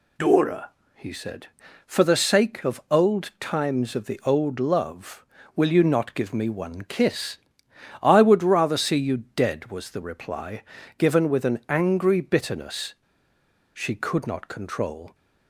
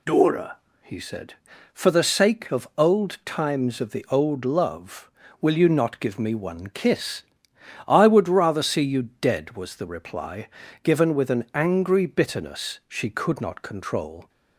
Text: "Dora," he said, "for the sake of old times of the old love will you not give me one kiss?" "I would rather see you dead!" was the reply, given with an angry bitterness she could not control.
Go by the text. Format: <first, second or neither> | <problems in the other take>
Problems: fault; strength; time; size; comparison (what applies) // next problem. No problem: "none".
second | pauses between "bitterness" and "she"; noticeable; at 12.9 s; 0.82 s long